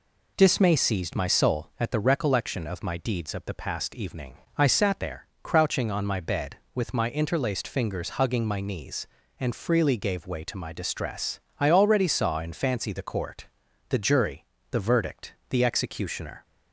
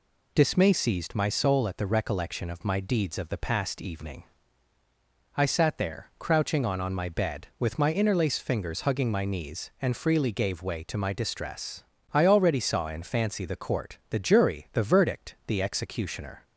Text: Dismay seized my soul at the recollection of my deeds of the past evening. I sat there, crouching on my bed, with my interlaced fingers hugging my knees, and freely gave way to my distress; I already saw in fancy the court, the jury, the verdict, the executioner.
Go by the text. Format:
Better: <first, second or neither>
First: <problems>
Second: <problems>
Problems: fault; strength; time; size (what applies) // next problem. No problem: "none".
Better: first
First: none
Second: says "on" twice; at 6.7 s